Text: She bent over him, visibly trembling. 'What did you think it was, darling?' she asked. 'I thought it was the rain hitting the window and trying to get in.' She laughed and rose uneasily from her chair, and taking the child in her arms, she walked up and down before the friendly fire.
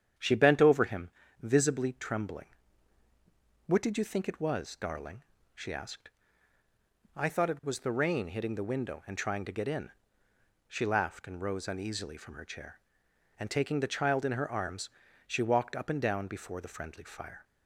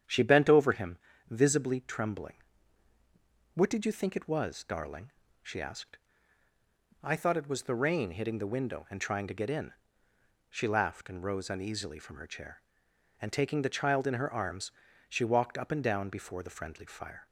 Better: neither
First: starts louder than the rest; strong; until 1.5 s; 8.5 dB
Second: starts louder than the rest; strong; until 1.3 s; 9 dB

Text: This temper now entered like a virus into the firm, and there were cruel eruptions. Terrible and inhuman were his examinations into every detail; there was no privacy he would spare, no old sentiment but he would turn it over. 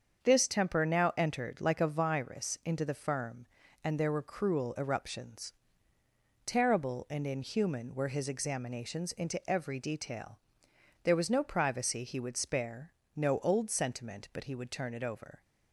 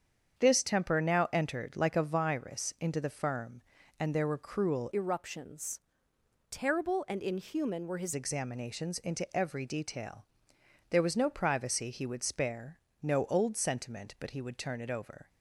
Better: first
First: starts louder than the rest; strong; until 1.2 s; 7 dB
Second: starts louder than the rest; strong; until 1.4 s; 8 dB // changes voice from "eruptions" to "his"; from 4.9 to 8.1 s; 3.2 s long

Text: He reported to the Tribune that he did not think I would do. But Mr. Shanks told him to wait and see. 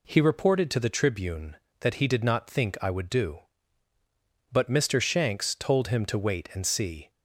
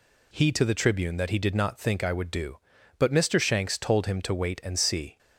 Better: first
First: none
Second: skips "reported"; at 0.5 s

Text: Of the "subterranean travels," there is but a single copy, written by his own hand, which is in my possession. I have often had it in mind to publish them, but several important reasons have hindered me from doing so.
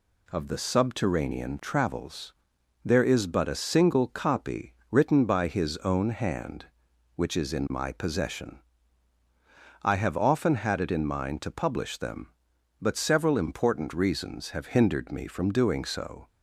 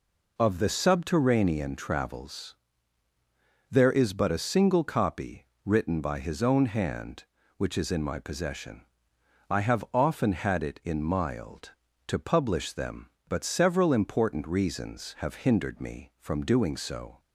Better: first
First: none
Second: says "mild" for "mind"; at 11.0 s

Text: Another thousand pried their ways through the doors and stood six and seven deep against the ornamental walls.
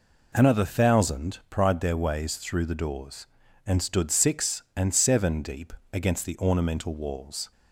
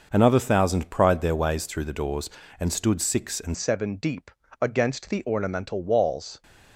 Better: first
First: pauses between "deep" and "against"; slight; at 5.7 s; 0.18 s long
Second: changes voice at "seven"; from 3.5 s on; 2.9 s long // pauses between "deep" and "against"; slight; at 4.3 s; 0.30 s long

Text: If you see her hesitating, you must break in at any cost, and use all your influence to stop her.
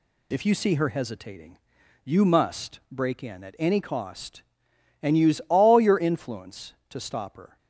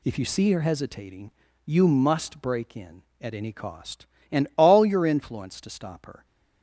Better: first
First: none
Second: skips "use"; at 4.5 s

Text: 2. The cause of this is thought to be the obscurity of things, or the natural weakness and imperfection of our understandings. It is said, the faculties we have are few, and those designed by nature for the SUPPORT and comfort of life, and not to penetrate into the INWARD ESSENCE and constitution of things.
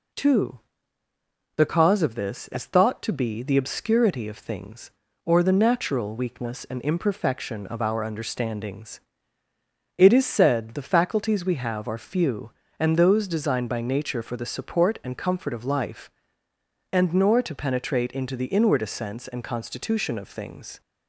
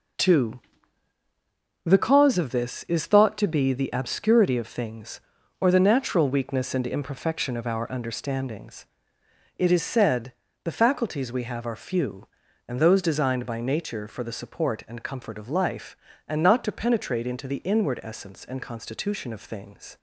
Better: second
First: says "nor" for "not"; at 17.1 s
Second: none

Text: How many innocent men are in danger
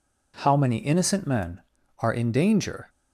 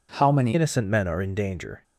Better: first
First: none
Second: changes voice at "innocent"; from 0.5 s on; 1.3 s long

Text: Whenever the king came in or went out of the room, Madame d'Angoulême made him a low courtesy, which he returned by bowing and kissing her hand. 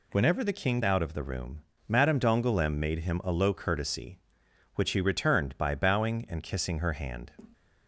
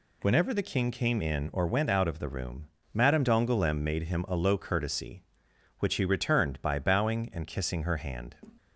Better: second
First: skips "came in or went"; at 0.8 s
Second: none

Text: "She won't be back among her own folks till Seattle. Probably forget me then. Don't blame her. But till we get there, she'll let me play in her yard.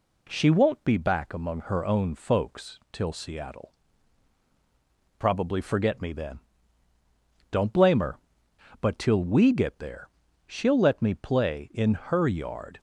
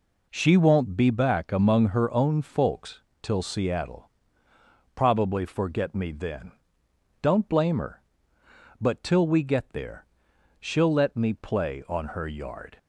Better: first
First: none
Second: pauses between "folks" and "till"; slight; at 3.0 s; 0.22 s long // says "on" for "in"; at 11.8 s

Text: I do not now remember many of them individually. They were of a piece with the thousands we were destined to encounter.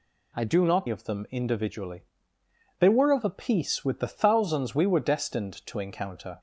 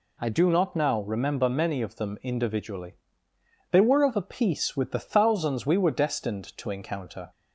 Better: second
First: skips "now remember many"; at 0.8 s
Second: none

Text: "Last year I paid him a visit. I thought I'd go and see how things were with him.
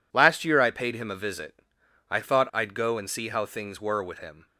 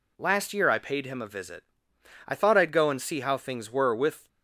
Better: first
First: none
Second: stops before "him"; at 4.2 s

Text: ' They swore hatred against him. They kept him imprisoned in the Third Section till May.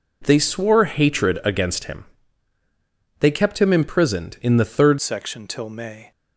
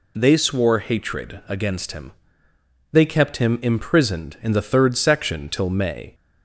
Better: second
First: changes voice at "Section"; from 5.0 s on; 1.1 s long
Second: none

